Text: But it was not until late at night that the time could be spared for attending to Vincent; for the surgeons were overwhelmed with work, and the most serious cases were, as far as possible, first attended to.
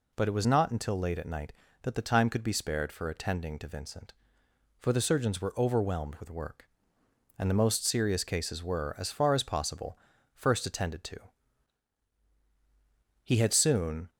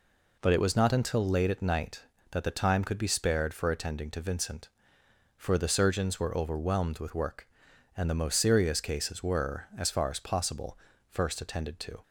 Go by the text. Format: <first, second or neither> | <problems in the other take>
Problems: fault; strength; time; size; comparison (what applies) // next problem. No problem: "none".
second | goes on to say "He had soon"; noticeable; from 13.2 s on; 0.86 s long